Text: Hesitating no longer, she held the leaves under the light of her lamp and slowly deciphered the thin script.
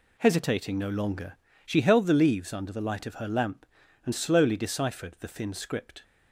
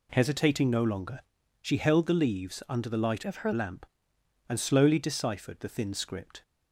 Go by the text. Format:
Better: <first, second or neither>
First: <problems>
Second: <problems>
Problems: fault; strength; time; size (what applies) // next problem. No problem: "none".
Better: first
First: none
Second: changes voice from "of" to "her"; from 3.2 to 3.5 s; 0.3 s long